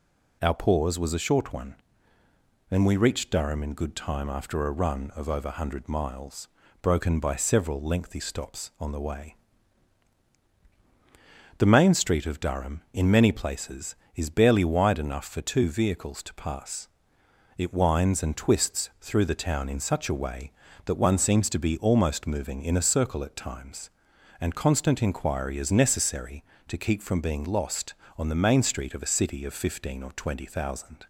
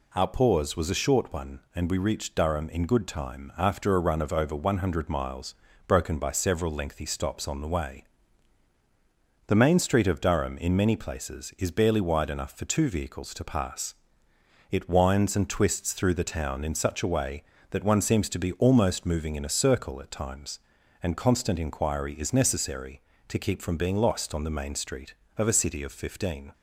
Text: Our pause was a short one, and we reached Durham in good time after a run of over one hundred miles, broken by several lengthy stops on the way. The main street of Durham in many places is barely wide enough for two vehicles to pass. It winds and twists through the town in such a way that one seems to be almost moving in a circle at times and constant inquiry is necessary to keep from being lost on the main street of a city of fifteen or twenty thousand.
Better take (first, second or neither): first